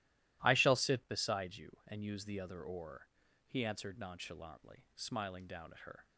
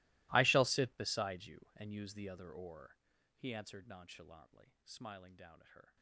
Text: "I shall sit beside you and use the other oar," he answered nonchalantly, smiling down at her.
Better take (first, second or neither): first